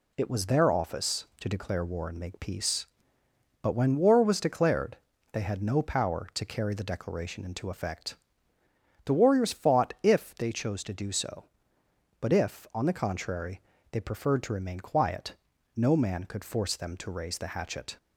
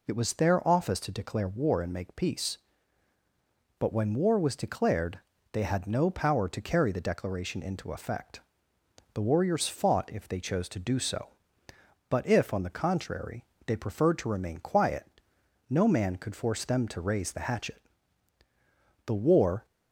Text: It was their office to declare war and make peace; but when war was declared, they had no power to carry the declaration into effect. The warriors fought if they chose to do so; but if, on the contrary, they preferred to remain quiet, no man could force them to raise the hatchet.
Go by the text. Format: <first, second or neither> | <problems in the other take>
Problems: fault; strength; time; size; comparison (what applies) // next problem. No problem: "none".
first | goes on to say "The war"; from 19.0 s on; 0.60 s long